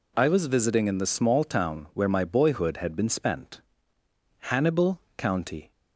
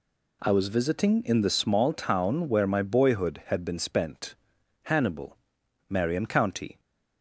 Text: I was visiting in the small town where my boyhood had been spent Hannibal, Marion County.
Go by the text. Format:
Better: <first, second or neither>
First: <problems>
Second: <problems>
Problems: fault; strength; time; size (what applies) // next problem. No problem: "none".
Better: second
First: pauses between "spent" and "Hannibal"; noticeable; at 3.6 s; 0.80 s long // skips "Marion"; at 5.0 s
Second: pauses between "spent" and "Hannibal"; noticeable; at 4.3 s; 0.48 s long